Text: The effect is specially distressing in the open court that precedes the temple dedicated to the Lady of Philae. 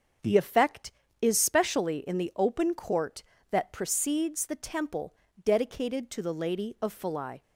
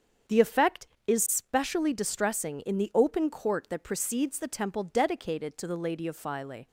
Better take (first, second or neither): second